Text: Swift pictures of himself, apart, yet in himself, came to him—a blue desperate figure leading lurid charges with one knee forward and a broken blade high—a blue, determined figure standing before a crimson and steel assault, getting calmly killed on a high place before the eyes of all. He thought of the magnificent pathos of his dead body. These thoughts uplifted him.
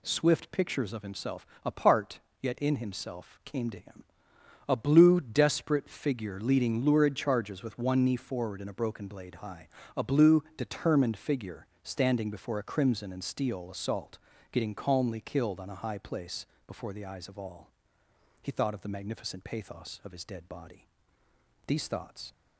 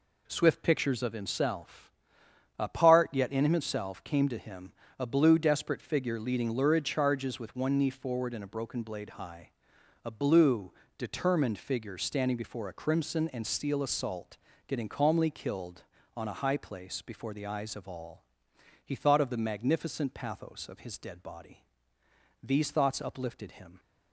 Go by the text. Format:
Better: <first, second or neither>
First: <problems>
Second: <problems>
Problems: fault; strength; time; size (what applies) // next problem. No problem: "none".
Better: second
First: pauses between "figure" and "standing"; slight; at 11.6 s; 0.18 s long // pauses between "place" and "before"; slight; at 16.4 s; 0.20 s long // stops before "uplifted him"; at 22.3 s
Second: none